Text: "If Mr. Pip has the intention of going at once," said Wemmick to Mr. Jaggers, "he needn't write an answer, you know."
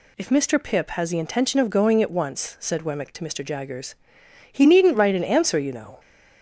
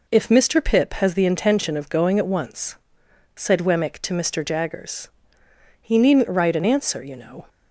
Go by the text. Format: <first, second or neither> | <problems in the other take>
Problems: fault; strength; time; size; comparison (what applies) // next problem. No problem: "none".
neither | none